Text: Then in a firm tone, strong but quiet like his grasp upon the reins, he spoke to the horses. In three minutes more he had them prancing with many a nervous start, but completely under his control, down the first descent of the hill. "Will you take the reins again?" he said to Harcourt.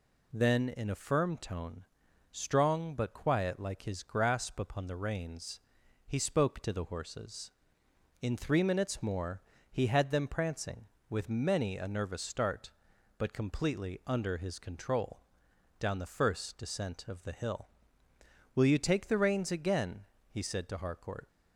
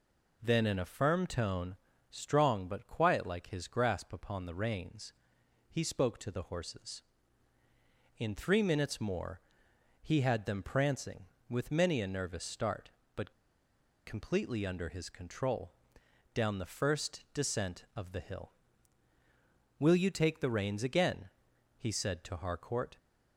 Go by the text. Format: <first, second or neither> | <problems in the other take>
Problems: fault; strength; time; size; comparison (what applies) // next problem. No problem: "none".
first | pauses between "more" and "he"; noticeable; at 9.4 s; 0.60 s long; slight in the first // pauses between "but" and "completely"; noticeable; at 13.3 s; 0.75 s long